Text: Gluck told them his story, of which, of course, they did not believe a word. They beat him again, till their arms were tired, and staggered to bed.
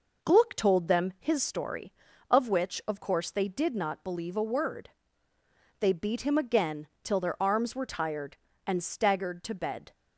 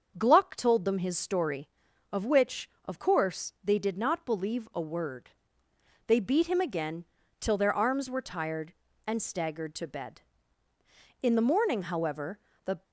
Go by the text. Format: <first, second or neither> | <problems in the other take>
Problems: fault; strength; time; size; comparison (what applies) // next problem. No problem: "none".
first | starts louder than the rest; until 1.1 s; 6.5 dB // goes on to say "In the morning however the"; from 11.2 s on; 1.6 s long